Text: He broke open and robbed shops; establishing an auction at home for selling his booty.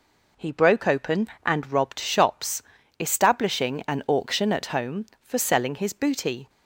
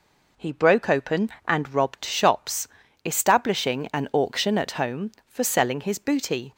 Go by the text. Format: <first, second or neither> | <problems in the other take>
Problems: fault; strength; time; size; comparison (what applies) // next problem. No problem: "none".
neither | none